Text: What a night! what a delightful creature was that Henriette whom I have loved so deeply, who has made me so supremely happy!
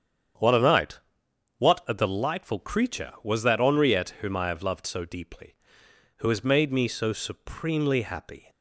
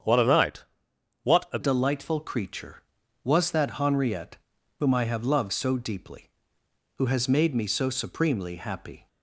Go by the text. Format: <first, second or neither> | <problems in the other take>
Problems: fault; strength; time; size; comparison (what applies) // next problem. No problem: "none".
first | starts louder than the rest; strong; until 1.7 s; 8 dB; strong in the first // changes voice at "delightful"; from 1.6 s on; 7.4 s long // pauses between "Henriette" and "whom"; at 4.3 s; 0.40 s long